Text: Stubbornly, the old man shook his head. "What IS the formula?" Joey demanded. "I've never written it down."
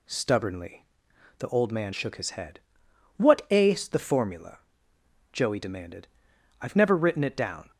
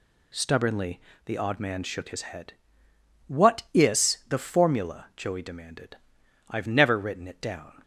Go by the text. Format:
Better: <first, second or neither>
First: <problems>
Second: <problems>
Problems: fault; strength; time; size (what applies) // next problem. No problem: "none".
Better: first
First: none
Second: says "odd" for "old"; at 1.3 s